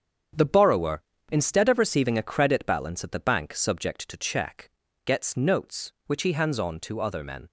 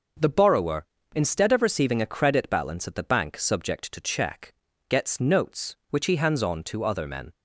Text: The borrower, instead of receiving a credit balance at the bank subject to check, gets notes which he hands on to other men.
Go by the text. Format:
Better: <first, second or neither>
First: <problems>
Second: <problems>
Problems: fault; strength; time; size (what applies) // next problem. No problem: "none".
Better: second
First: gets quieter; strong; throughout; 9 dB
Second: none